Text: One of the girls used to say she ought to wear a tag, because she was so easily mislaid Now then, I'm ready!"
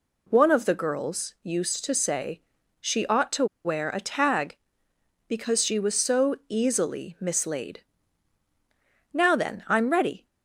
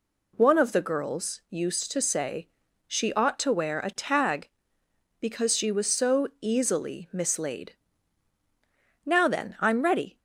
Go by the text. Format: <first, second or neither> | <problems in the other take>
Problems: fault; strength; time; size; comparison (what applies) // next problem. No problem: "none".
second | pauses between "say" and "she"; at 2.4 s; 0.40 s long; also in the second // pauses between "to" and "wear"; slight; at 3.4 s; 0.19 s long // pauses between "mislaid" and "Now"; strong; at 7.8 s; 1.3 s long; strong in the second